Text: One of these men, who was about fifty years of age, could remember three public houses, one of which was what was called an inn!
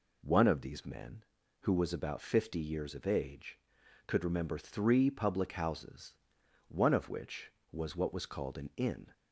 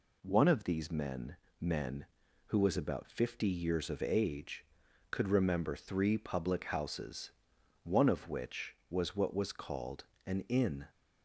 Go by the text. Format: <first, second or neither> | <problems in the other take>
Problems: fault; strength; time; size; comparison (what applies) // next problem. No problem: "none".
first | says "men" twice; at 1.5 s // pauses between "called" and "an"; slight; at 10.0 s; 0.20 s long